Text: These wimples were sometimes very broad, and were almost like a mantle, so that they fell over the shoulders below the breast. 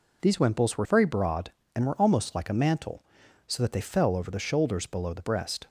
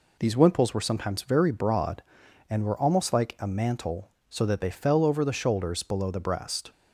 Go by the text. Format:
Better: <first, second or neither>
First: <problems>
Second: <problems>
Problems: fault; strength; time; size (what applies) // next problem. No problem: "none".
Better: second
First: skips "sometimes"; at 0.8 s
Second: none